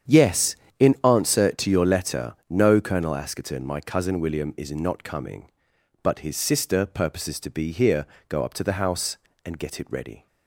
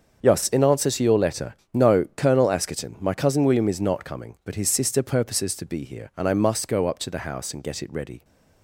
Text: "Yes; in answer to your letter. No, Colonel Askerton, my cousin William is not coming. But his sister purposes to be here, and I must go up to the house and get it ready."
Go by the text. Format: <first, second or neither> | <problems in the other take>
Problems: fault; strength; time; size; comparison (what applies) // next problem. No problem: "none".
second | starts louder than the rest; strong; until 1.4 s; 8.5 dB; also in the second // skips "and I must"; at 8.1 s